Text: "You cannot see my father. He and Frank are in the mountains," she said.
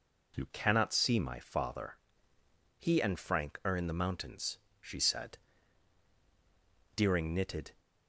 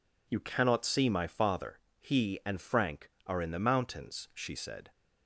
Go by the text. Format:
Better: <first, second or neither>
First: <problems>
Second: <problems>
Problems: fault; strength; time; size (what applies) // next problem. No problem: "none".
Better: second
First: goes on to say "Deering knitted"; noticeable; from 6.9 s on; 0.74 s long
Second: none